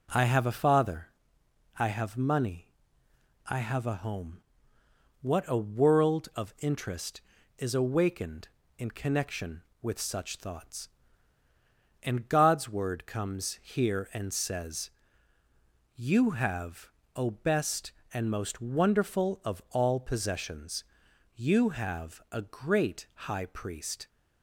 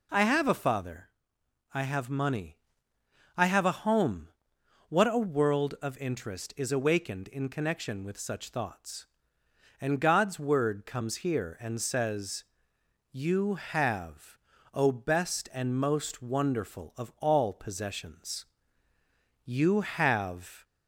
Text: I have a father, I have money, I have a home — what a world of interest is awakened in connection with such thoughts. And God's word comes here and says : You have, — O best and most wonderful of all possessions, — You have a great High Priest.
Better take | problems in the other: first | stops before "a great High Priest"; at 20.6 s

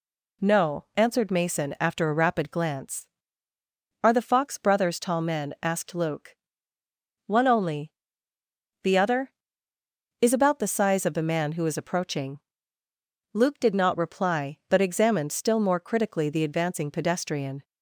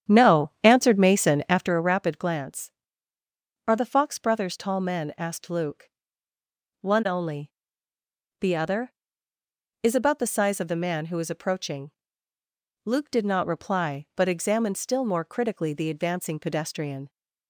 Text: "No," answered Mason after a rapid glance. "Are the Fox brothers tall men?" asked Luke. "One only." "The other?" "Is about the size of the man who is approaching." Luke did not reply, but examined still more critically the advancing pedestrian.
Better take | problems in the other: first | starts louder than the rest; strong; until 1.7 s; 9.5 dB

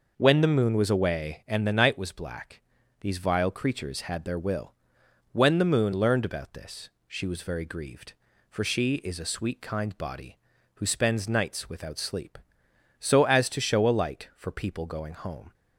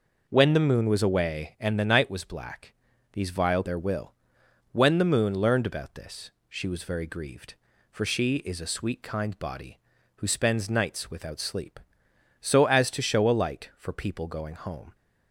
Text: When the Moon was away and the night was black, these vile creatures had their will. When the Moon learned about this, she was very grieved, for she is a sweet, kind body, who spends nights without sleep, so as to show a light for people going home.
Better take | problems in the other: first | skips "creatures had"; at 3.6 s

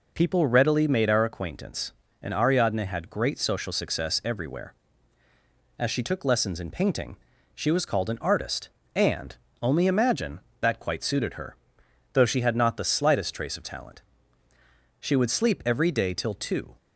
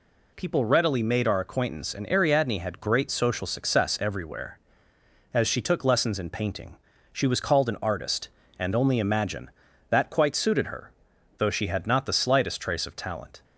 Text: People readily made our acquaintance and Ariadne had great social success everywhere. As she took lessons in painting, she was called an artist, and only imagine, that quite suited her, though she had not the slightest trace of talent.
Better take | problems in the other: second | pauses between "and" and "only"; slight; at 9.3 s; 0.26 s long // goes on to say "She would sleep every day till two"; strong; from 15.0 s on; 1.7 s long

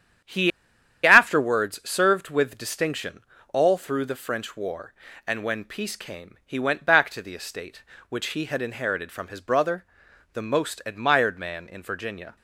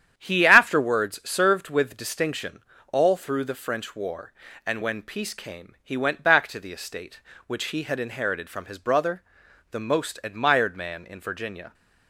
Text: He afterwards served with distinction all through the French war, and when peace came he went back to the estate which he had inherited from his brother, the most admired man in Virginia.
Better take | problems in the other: second | starts louder than the rest; strong; until 1.8 s; 9 dB; strong in the second // pauses between "He" and "afterwards"; noticeable; at 0.5 s; 0.55 s long // pauses between "distinction" and "all"; slight; at 3.2 s; 0.32 s long; slight in the second

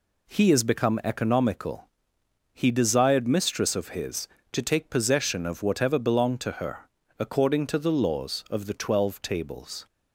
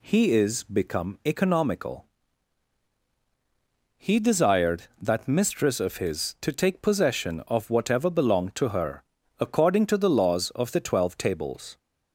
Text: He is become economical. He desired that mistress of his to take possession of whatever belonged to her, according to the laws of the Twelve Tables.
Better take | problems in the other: second | skips "that"; at 3.2 s

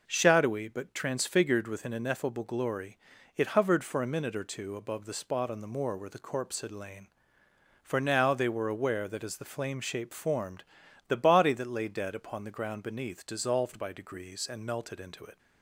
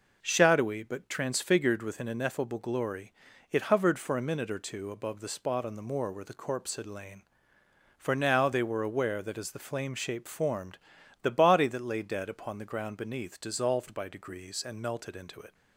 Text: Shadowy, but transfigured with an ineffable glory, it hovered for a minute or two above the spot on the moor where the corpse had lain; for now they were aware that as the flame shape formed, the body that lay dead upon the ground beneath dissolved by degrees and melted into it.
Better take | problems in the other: neither | none

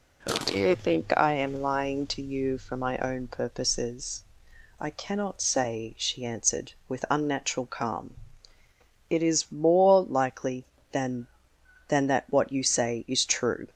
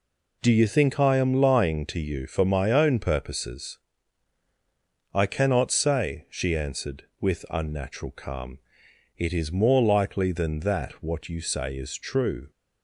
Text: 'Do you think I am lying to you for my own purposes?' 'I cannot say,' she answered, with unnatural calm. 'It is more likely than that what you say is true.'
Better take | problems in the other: second | says "than" twice; at 11.8 s

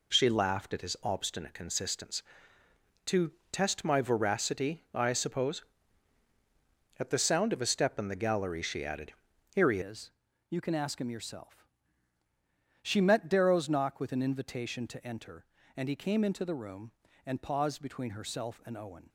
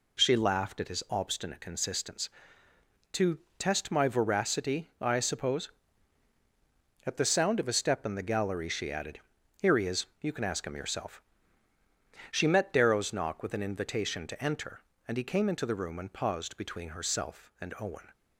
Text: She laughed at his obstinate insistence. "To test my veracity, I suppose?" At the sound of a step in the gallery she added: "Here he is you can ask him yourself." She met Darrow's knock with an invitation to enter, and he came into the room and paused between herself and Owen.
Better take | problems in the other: second | pauses between "To" and "test"; slight; at 3.3 s; 0.22 s long; slight in the second // changes voice at "is"; from 9.8 s on; 9.2 s long // pauses between "is" and "you"; at 10.1 s; 0.40 s long

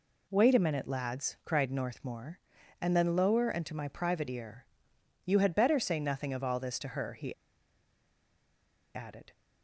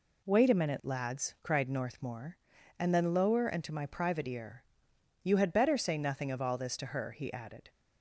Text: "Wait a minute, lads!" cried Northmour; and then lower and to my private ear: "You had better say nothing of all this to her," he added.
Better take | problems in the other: second | pauses between "he" and "added"; strong; at 7.3 s; 1.6 s long

